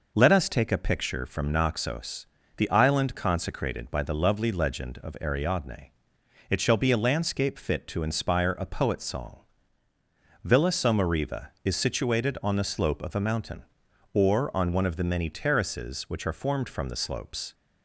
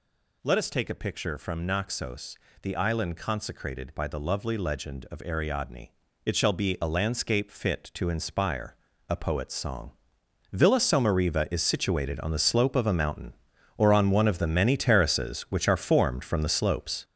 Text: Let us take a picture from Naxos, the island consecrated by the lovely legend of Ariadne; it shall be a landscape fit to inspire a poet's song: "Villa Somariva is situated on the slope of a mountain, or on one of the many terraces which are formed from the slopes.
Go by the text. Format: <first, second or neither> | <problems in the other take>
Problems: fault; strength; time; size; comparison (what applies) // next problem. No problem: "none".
first | gets louder; strong; throughout; 8 dB // pauses between "inspire" and "a"; slight; at 8.7 s; 0.36 s long